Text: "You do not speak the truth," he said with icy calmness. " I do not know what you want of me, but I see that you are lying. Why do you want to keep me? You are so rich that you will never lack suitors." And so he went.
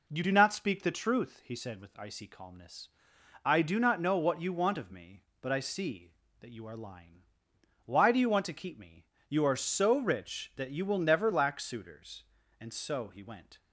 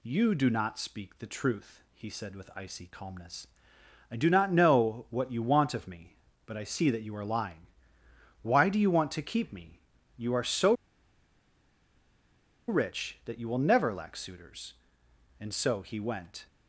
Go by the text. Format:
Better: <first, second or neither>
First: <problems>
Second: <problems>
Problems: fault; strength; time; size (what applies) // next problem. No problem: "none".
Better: first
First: none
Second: pauses between "so" and "rich"; strong; at 10.7 s; 1.9 s long